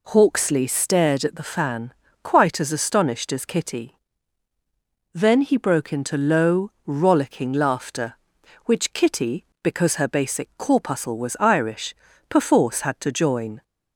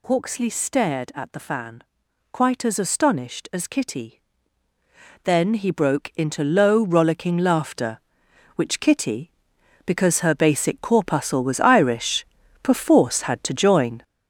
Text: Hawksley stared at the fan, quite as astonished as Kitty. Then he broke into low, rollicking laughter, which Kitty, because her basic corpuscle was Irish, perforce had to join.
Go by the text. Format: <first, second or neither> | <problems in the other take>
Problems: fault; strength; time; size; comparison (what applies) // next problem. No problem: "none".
first | gets louder; strong; throughout; 7.5 dB